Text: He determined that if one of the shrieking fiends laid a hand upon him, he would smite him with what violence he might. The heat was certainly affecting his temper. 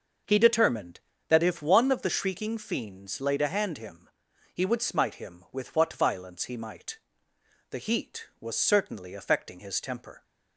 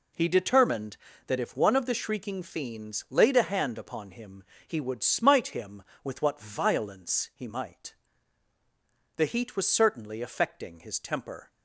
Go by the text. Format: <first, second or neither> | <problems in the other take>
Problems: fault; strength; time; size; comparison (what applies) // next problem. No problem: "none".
second | starts louder than the rest; noticeable; until 1.5 s; 6 dB // skips "upon"; at 3.7 s